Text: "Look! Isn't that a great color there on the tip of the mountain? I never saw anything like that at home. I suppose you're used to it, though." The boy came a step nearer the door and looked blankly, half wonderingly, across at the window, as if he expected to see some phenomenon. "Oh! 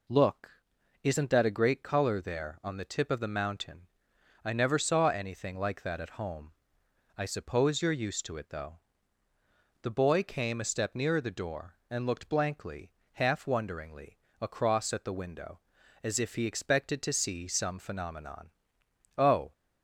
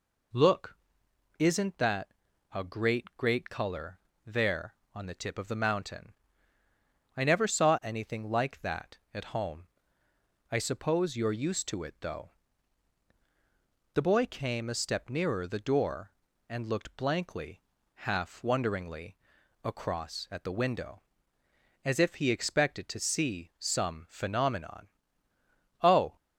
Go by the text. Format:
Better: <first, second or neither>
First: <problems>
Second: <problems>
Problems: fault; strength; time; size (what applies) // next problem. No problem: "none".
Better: first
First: none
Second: pauses between "that" and "a"; noticeable; at 2.0 s; 0.46 s long // says "great" twice; at 3.1 s // pauses between "color" and "there"; slight; at 3.9 s; 0.26 s long